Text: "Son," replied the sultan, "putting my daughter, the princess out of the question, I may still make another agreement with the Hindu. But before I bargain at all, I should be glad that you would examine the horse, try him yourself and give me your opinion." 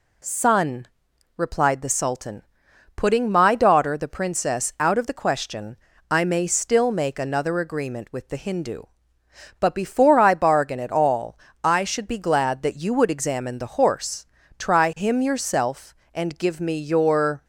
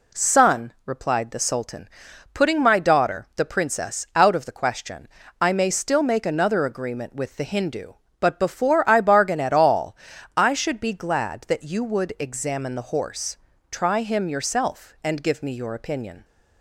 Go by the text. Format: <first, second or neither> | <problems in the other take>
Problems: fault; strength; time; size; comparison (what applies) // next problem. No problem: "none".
second | stops before "opinion"; at 17.4 s